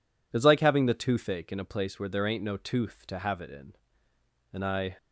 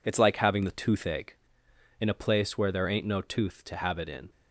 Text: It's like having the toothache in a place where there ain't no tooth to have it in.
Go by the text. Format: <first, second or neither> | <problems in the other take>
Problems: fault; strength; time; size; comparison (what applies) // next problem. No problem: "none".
second | goes on to say "And I"; slight; from 4.5 s on; 0.44 s long